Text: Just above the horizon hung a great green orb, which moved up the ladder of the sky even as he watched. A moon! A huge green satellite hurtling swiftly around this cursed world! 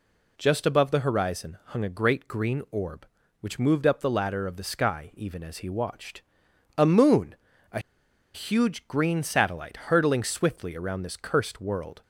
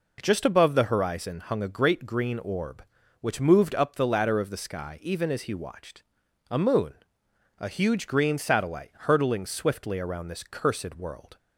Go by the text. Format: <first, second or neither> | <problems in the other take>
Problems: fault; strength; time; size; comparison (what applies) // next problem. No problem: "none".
second | pauses between "A" and "huge"; noticeable; at 7.7 s; 0.54 s long